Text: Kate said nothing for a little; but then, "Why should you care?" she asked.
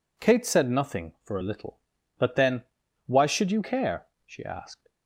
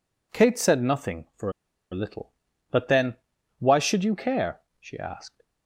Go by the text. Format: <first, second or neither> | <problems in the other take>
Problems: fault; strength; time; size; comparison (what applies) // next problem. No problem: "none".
first | pauses between "for" and "a"; at 1.4 s; 0.41 s long